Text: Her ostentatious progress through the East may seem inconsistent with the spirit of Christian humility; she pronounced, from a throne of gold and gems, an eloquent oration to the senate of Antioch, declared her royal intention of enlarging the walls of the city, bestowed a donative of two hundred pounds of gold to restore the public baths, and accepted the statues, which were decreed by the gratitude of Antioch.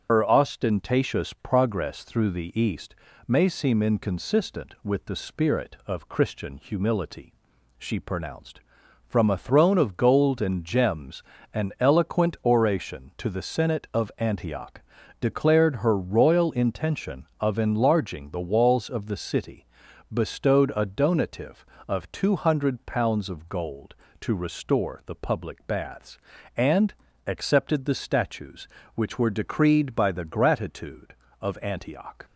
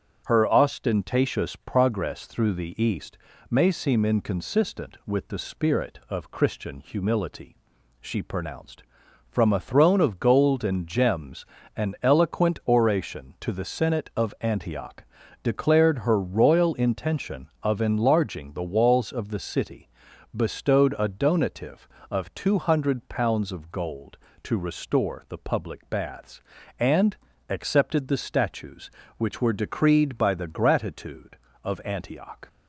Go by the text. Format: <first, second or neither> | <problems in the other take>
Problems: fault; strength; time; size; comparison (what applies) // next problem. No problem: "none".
second | loses the start of "Her"; at 0.0 s; 70 ms // starts louder than the rest; strong; until 1.1 s; 7.5 dB; strong in the second // pauses between "East" and "may"; slight; at 2.9 s; 0.32 s long; slight in the second // pauses between "and" and "accepted"; slight; at 26.9 s; 0.32 s long; slight in the second